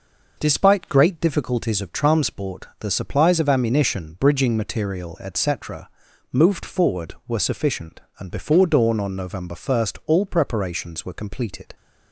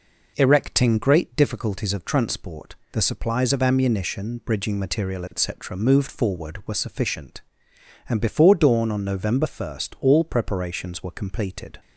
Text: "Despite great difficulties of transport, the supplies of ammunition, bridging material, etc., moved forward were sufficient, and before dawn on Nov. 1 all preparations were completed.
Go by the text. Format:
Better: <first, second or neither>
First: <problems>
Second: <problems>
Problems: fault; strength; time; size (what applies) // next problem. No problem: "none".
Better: first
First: none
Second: says "Erecting" for "Despite"; at 0.3 s